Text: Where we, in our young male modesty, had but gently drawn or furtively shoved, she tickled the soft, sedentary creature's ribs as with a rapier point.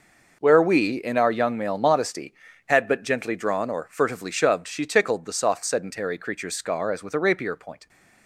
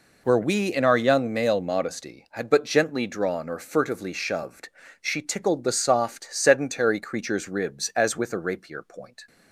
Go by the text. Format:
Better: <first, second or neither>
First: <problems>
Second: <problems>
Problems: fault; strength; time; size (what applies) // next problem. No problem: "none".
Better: second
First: says "scar" for "ribs"; at 6.5 s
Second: none